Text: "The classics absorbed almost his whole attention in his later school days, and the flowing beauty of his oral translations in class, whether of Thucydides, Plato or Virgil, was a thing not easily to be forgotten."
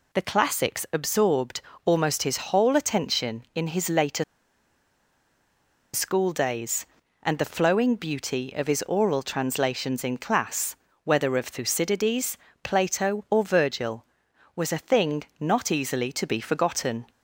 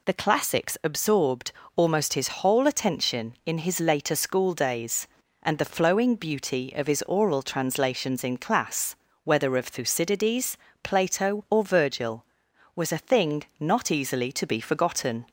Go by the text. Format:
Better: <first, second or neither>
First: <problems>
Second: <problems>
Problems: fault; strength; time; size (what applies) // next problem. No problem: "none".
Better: second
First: pauses between "absorbed" and "almost"; slight; at 1.6 s; 0.24 s long // pauses between "his" and "whole"; slight; at 2.3 s; 0.16 s long // pauses between "later" and "school"; strong; at 4.2 s; 1.7 s long // pauses between "thing" and "not"; slight; at 15.2 s; 0.16 s long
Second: pauses between "absorbed" and "almost"; slight; at 1.5 s; 0.24 s long // pauses between "his" and "whole"; slight; at 2.2 s; 0.16 s long // pauses between "thing" and "not"; slight; at 13.4 s; 0.16 s long